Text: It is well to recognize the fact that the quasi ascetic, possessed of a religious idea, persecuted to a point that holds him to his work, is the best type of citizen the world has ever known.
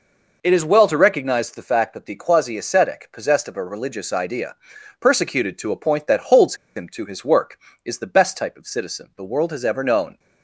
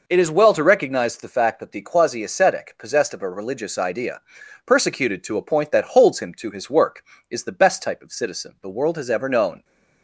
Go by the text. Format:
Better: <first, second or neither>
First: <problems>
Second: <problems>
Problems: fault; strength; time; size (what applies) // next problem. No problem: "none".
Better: second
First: pauses between "holds" and "him"; slight; at 6.5 s; 0.21 s long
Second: none